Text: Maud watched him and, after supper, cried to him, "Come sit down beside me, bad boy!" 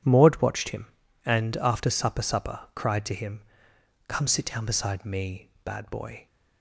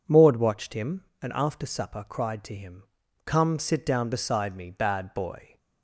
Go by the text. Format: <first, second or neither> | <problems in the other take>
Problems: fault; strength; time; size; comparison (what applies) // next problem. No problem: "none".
second | says "supper" twice; at 2.2 s